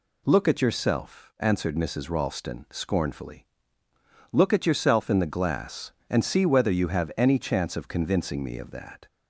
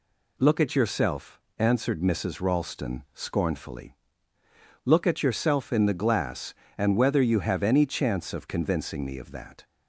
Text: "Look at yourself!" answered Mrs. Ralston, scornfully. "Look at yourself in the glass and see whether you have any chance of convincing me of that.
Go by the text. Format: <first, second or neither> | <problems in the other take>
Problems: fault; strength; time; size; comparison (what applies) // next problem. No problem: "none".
first | skips "see"; at 6.9 s